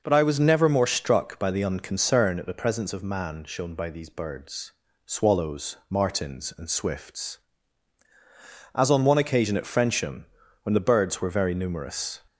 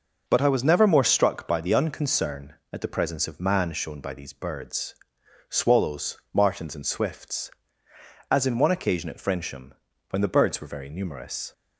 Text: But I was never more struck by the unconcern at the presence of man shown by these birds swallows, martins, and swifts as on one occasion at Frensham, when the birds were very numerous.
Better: first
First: pauses between "birds" and "swallows"; at 4.7 s; 0.38 s long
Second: pauses between "birds" and "swallows"; noticeable; at 4.9 s; 0.54 s long // says "in" for "on"; at 8.4 s

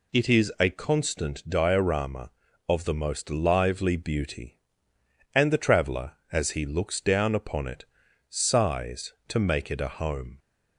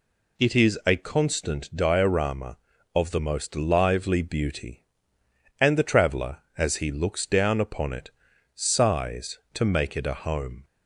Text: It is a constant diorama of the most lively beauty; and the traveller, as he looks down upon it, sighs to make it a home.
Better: neither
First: none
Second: none

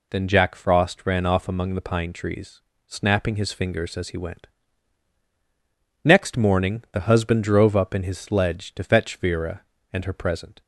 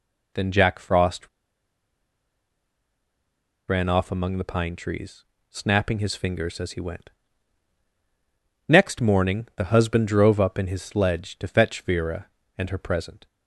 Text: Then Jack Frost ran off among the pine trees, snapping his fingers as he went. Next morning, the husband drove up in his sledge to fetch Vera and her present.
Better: first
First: none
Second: pauses between "Frost" and "ran"; strong; at 1.2 s; 2.3 s long

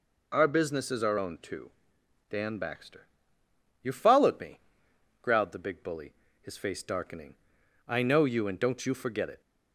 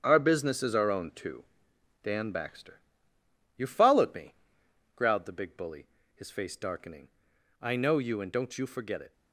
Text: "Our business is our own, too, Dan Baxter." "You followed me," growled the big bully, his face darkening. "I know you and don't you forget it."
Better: first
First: none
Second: gets quieter; strong; throughout; 8.5 dB

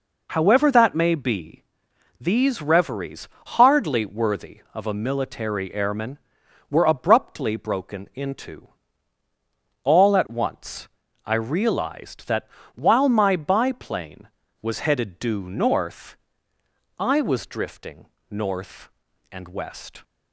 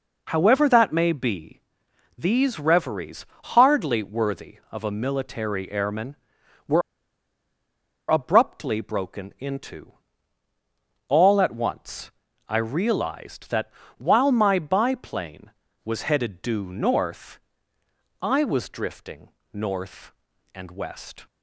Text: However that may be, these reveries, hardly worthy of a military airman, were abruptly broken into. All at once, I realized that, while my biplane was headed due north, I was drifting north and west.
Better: first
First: pauses between "drifting" and "north"; slight; at 18.0 s; 0.22 s long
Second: pauses between "were" and "abruptly"; strong; at 6.8 s; 1.2 s long // pauses between "drifting" and "north"; slight; at 19.2 s; 0.22 s long

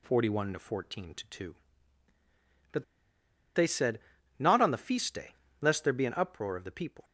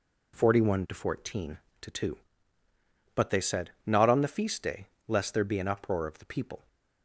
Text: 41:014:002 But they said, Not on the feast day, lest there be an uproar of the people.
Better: second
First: pauses between "But" and "they"; noticeable; at 2.8 s; 0.70 s long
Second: none

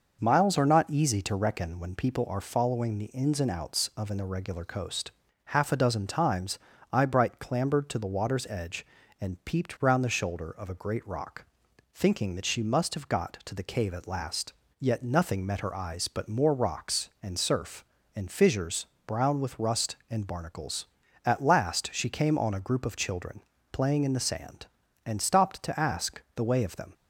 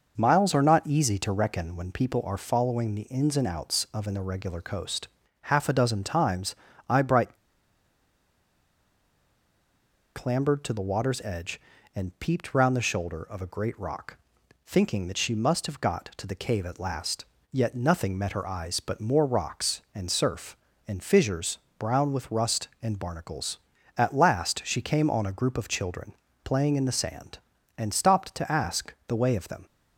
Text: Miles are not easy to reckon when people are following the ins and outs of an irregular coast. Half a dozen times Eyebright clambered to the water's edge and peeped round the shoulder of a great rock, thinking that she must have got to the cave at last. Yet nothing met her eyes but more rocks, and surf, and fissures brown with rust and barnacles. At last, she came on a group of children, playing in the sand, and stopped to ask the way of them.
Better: first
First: pauses between "times" and "Eyebright"; slight; at 6.5 s; 0.34 s long // pauses between "fissures" and "brown"; slight; at 18.8 s; 0.22 s long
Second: pauses between "times" and "Eyebright"; slight; at 6.5 s; 0.34 s long // pauses between "Eyebright" and "clambered"; strong; at 7.3 s; 2.7 s long // pauses between "fissures" and "brown"; slight; at 21.5 s; 0.22 s long

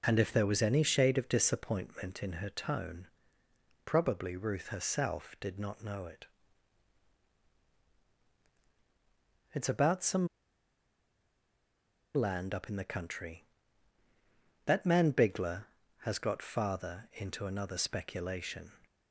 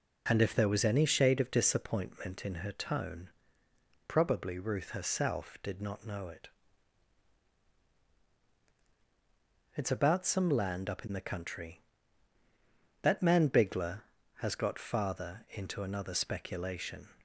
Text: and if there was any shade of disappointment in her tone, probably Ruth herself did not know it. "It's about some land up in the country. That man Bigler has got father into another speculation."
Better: second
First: pauses between "some" and "land"; strong; at 10.2 s; 1.8 s long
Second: none

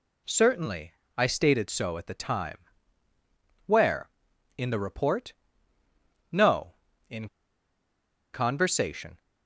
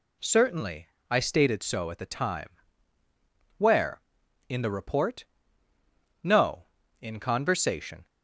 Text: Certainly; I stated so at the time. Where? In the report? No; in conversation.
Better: second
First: pauses between "in" and "conversation"; at 7.2 s; 1.0 s long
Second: none

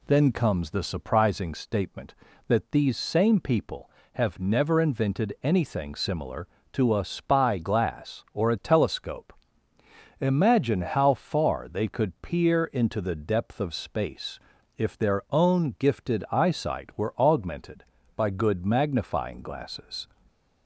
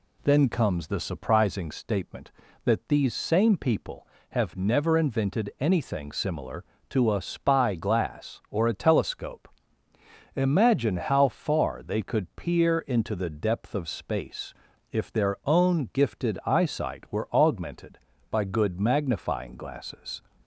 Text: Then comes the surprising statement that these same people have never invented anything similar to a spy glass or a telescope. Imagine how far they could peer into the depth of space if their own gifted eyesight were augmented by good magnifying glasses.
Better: neither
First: pauses between "space" and "if"; at 14.3 s; 0.38 s long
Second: pauses between "space" and "if"; at 14.5 s; 0.38 s long

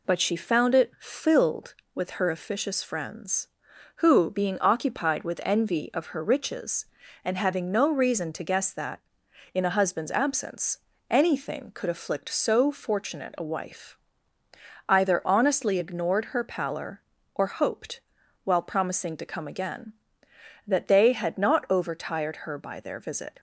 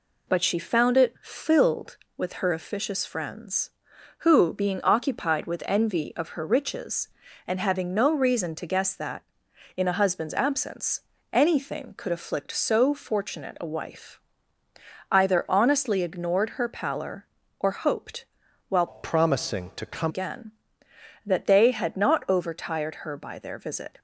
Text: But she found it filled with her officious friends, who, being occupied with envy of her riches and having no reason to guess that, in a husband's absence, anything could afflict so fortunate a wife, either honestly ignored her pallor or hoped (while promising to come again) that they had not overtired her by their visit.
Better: first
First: none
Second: changes voice from "promising" to "come"; from 18.8 to 20.1 s; 1.3 s long

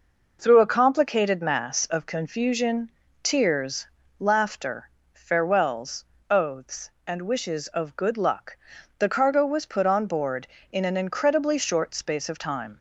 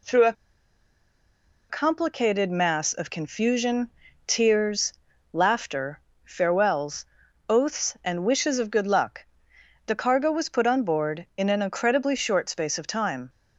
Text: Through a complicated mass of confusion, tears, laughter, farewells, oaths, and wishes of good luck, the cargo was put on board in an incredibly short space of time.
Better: first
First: none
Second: pauses between "a" and "complicated"; strong; at 0.3 s; 1.3 s long

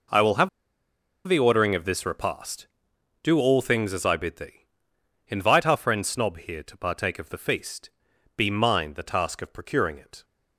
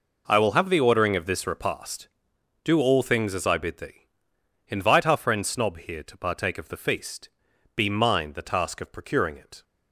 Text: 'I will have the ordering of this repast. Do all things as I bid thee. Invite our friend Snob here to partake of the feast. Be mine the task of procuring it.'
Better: second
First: pauses between "have" and "the"; noticeable; at 0.4 s; 0.78 s long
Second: none

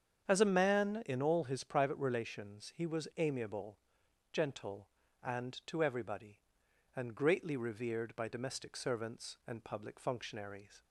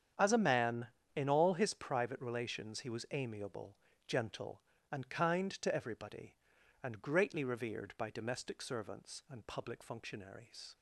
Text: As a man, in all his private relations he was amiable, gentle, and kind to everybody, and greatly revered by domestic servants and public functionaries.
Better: second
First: starts louder than the rest; strong; until 1.2 s; 7.5 dB // skips "kind"; at 5.6 s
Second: starts louder than the rest; strong; until 1.4 s; 8.5 dB

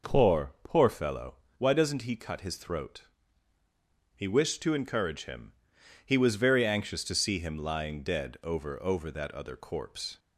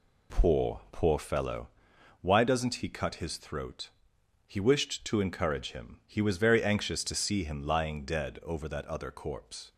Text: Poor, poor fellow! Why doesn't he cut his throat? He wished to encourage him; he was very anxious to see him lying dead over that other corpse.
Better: second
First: says "over" twice; at 8.8 s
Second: none

